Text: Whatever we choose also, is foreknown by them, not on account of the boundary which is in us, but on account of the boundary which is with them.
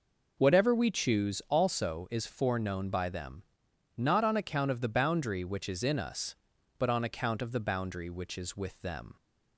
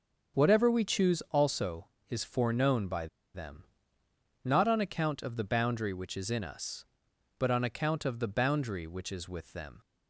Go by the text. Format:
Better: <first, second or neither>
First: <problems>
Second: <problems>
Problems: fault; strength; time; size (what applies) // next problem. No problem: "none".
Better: first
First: none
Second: starts louder than the rest; until 1.4 s; 7 dB // pauses between "by" and "them"; slight; at 3.0 s; 0.27 s long